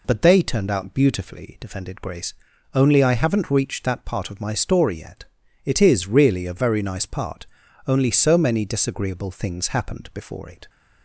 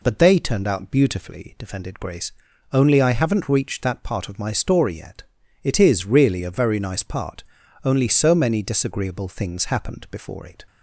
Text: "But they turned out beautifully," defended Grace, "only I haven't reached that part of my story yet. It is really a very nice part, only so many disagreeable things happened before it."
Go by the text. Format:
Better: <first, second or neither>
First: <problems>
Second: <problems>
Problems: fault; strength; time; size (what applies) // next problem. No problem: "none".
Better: neither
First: none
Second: none